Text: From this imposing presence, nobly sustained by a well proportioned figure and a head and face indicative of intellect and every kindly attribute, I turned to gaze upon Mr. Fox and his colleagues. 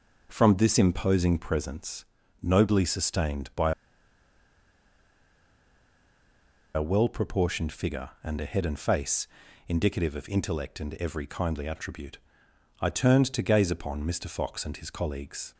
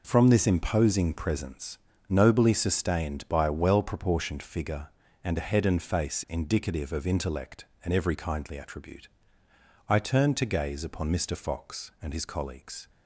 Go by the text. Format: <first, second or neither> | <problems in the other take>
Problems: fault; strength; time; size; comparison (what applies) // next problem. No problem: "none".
second | pauses between "by" and "a"; strong; at 3.7 s; 3.0 s long // pauses between "face" and "indicative"; at 9.2 s; 0.42 s long